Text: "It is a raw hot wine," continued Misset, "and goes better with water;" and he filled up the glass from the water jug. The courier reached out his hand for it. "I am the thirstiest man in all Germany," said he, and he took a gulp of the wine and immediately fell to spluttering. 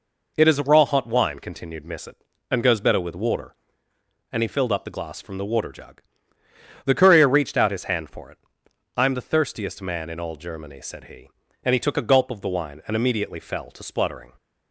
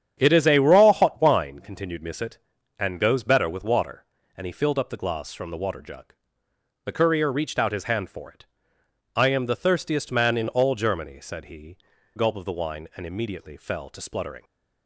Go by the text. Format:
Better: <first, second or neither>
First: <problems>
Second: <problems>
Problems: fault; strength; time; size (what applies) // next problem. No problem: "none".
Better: first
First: none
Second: starts louder than the rest; strong; until 1.1 s; 8.5 dB // skips "and he took a"; at 11.9 s